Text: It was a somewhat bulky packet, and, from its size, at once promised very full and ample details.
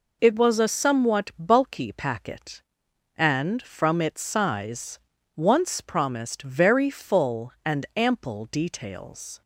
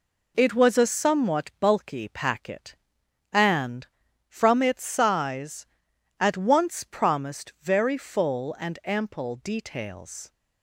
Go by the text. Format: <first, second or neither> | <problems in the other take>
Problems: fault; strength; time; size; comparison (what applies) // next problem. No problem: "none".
second | skips "at"; at 5.1 s